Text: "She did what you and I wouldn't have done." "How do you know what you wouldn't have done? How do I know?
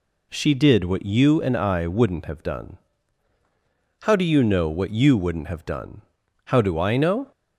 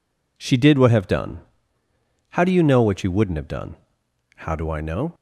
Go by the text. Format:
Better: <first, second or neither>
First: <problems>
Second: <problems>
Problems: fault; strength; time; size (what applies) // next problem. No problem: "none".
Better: first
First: none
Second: skips "you and I wouldn't"; at 0.9 s